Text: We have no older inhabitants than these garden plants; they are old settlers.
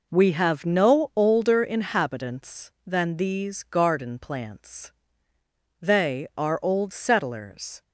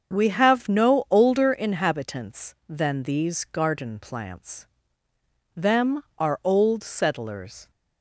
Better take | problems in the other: first | starts louder than the rest; until 1.1 s; 7 dB // says "them" for "they"; at 5.5 s

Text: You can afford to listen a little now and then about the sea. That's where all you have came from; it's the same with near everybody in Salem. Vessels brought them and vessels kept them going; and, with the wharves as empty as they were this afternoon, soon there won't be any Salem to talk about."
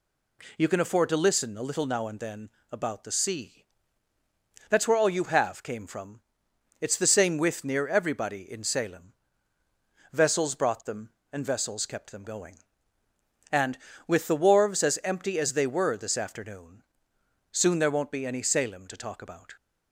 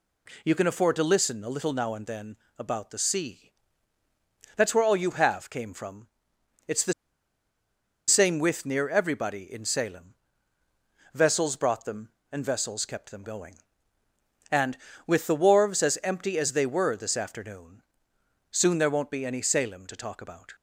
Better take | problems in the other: first | pauses between "then" and "about"; slight; at 2.3 s; 0.22 s long; slight in the first // pauses between "the" and "same"; at 6.9 s; 1.1 s long

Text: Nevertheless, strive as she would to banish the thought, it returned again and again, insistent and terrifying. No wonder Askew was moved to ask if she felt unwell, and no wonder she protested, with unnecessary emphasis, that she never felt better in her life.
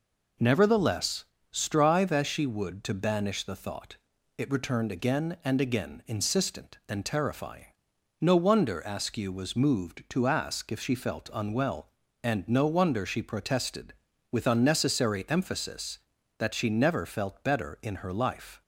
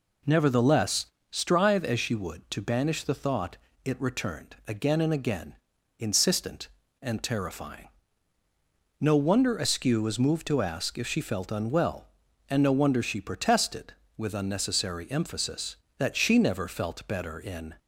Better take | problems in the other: first | stops before "her life"; at 17.7 s

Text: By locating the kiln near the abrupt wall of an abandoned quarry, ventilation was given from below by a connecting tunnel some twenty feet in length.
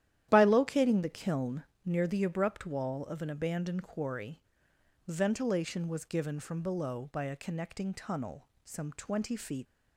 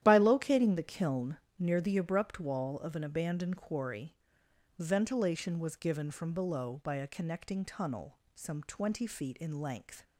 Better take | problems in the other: second | starts louder than the rest; strong; until 1.3 s; 11.5 dB; strong in the second // pauses between "kiln" and "near"; slight; at 1.6 s; 0.24 s long; slight in the second // pauses between "tunnel" and "some"; slight; at 8.4 s; 0.16 s long; slight in the second // stops before "in length"; at 9.6 s

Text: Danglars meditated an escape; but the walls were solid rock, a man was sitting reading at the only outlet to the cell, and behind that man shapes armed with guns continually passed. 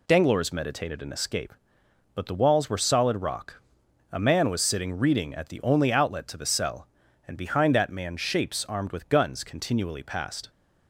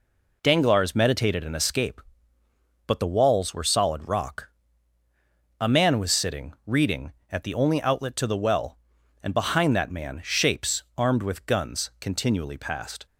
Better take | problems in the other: first | says "well" for "cell"; at 8.3 s

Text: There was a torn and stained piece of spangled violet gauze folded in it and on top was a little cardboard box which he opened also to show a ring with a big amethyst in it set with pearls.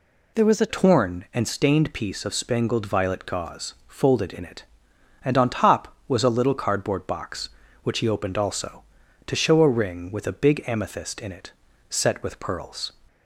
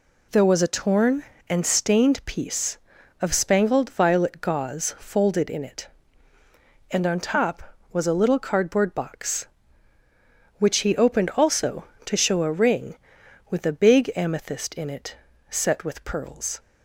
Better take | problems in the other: second | changes voice at "torn"; from 0.6 s on; 12.3 s long // pauses between "it" and "set"; slight; at 11.5 s; 0.36 s long; slight in the second

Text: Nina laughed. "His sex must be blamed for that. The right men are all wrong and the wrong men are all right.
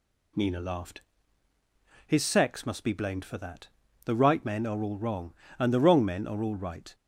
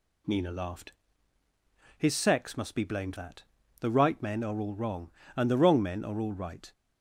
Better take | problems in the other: first | skips "for"; at 3.1 s

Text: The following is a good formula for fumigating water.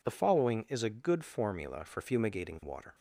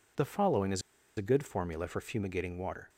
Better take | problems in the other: first | pauses between "is" and "a"; slight; at 0.8 s; 0.35 s long

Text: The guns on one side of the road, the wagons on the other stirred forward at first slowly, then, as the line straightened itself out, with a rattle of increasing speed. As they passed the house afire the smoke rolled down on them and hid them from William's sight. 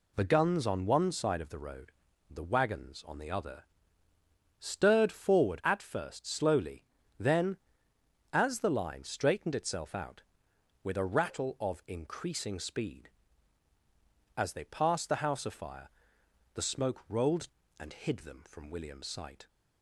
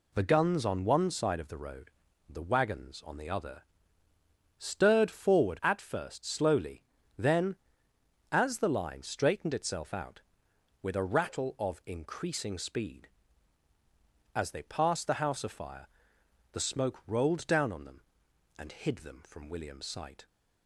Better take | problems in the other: second | pauses between "other" and "stirred"; noticeable; at 3.6 s; 0.96 s long; noticeable in the second // pauses between "afire" and "the"; noticeable; at 15.8 s; 0.66 s long; noticeable in the second // skips "down on them"; at 17.6 s

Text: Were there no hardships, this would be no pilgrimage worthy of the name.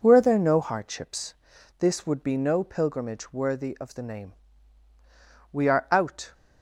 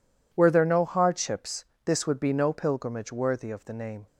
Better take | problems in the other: second | goes on to say "We are out"; noticeable; from 5.5 s on; 0.80 s long

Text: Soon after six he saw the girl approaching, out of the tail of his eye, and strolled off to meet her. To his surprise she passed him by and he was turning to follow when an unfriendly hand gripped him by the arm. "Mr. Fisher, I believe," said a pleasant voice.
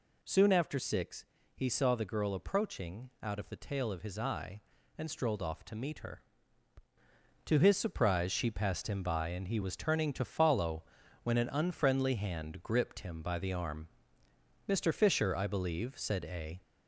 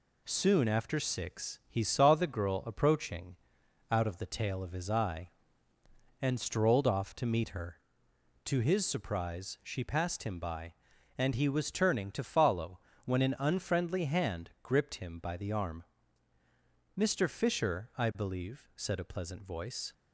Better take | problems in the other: second | pauses between "six" and "he"; slight; at 1.2 s; 0.32 s long // pauses between "follow" and "when"; at 10.8 s; 0.40 s long; slight in the second // stops before "pleasant voice"; at 16.6 s

